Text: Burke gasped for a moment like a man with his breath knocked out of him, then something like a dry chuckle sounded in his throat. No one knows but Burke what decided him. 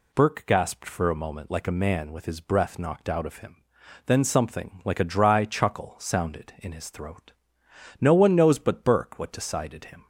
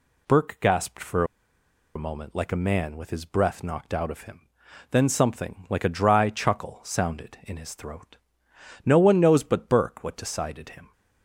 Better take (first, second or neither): first